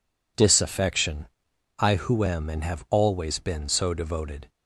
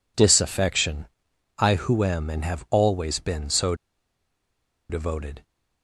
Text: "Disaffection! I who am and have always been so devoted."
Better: first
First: none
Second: pauses between "so" and "devoted"; at 3.7 s; 1.1 s long

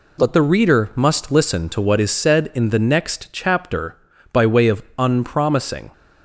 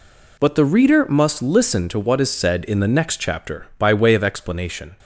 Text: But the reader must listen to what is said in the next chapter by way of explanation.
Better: second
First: says "unpromising" for "explanation"; at 4.9 s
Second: none

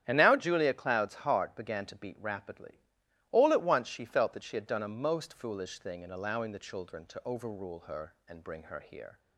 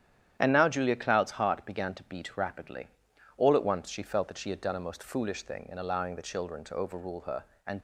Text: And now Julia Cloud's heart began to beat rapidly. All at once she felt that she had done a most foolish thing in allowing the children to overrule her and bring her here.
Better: first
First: starts louder than the rest; strong; until 1.0 s; 10 dB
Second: starts louder than the rest; strong; until 1.4 s; 10 dB // stops before "bring her here"; at 7.7 s

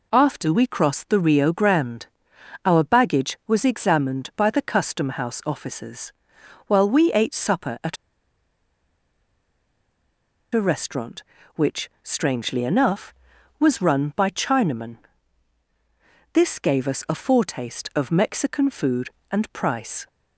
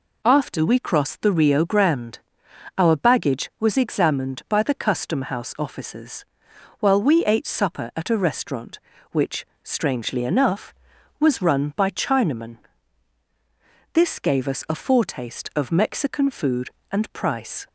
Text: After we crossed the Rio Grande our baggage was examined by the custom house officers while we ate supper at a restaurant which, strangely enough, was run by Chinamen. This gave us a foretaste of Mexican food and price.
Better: second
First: pauses between "Grande" and "our"; noticeable; at 2.0 s; 0.58 s long // pauses between "officers" and "while"; noticeable; at 6.1 s; 0.54 s long // pauses between "at" and "a"; strong; at 7.9 s; 2.5 s long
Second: pauses between "Grande" and "our"; noticeable; at 2.1 s; 0.58 s long // pauses between "officers" and "while"; noticeable; at 6.2 s; 0.54 s long

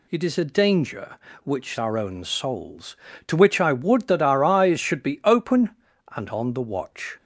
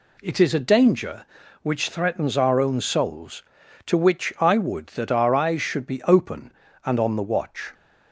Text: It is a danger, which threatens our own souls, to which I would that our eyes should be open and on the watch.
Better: second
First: skips "threatens"; at 1.7 s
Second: none

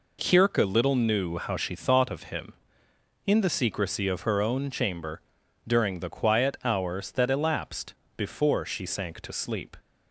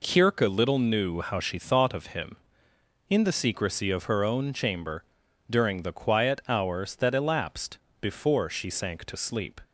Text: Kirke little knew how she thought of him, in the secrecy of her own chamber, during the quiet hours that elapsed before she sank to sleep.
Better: neither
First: pauses between "elapsed" and "before"; slight; at 7.9 s; 0.22 s long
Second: pauses between "elapsed" and "before"; slight; at 7.7 s; 0.22 s long

